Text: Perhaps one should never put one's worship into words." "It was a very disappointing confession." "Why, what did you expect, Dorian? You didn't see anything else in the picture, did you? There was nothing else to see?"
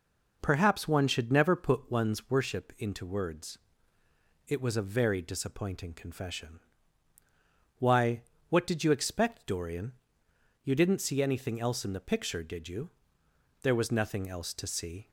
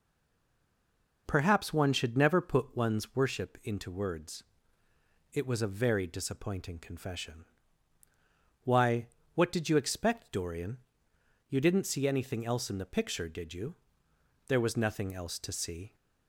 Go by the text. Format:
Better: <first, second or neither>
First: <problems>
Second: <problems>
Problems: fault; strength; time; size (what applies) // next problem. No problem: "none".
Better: first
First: none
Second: stays silent before the first word; noticeable; until 1.2 s; 1.2 s long